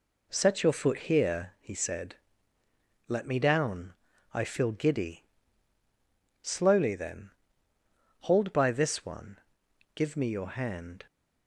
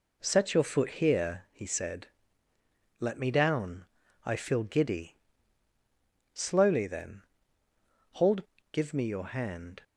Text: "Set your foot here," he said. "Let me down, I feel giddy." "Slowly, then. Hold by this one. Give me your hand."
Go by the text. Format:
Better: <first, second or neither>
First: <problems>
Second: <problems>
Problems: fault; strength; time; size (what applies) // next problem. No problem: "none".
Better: first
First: none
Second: skips "by this one"; at 8.5 s